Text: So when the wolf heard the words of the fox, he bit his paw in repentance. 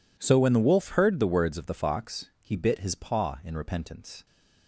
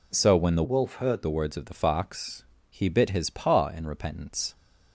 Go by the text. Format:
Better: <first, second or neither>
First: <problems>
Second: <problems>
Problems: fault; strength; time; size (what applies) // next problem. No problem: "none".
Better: first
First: none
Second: changes voice from "wolf" to "heard"; from 0.6 to 1.2 s; 0.6 s long